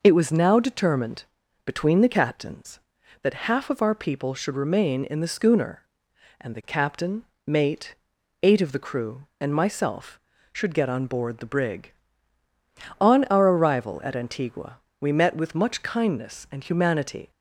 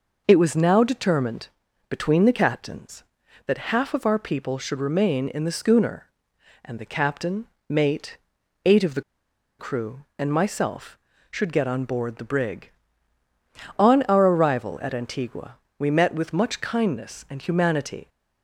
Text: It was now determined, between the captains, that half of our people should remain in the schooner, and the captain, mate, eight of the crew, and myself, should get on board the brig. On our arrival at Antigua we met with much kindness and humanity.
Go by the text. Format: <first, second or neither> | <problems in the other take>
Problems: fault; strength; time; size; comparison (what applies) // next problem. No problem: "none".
first | pauses between "the" and "crew"; noticeable; at 9.0 s; 0.58 s long // pauses between "Antigua" and "we"; slight; at 15.5 s; 0.24 s long; slight in the first